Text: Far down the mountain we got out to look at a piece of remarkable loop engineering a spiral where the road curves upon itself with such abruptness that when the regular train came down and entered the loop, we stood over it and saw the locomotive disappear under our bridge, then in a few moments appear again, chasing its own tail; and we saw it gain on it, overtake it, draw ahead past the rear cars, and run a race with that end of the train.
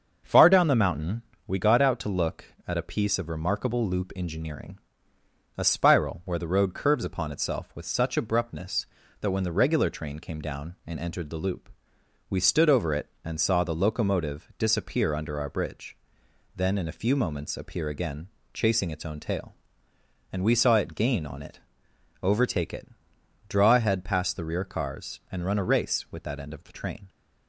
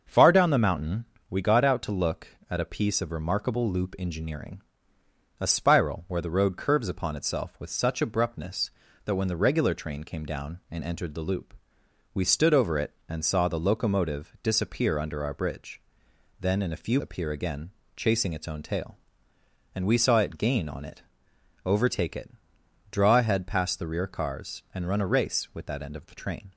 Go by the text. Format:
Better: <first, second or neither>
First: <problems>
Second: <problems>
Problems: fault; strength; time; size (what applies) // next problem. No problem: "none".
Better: first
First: starts louder than the rest; until 1.5 s; 6.5 dB // pauses between "mountain" and "we"; slight; at 1.2 s; 0.26 s long // pauses between "engineering" and "a"; noticeable; at 4.7 s; 0.78 s long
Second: starts louder than the rest; until 1.3 s; 6.5 dB // pauses between "mountain" and "we"; slight; at 1.0 s; 0.26 s long // pauses between "engineering" and "a"; noticeable; at 4.6 s; 0.78 s long // skips "moments"; at 16.9 s